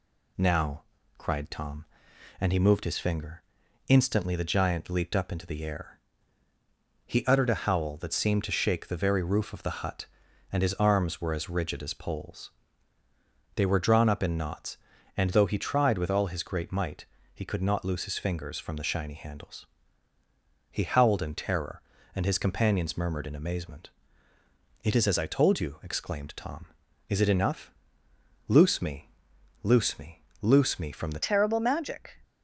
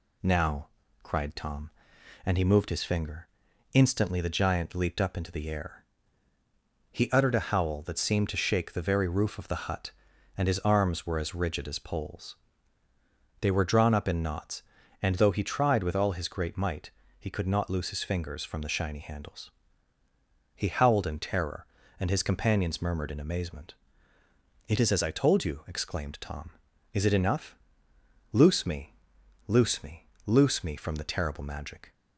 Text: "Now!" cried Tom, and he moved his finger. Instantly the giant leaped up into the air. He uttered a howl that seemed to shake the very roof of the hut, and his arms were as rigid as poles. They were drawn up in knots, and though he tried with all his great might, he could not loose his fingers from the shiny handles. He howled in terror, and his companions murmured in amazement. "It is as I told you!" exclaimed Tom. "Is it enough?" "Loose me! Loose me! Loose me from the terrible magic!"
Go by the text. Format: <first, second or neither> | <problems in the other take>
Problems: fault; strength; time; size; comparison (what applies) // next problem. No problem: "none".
second | changes voice at "terrible"; from 31.2 s on; 0.9 s long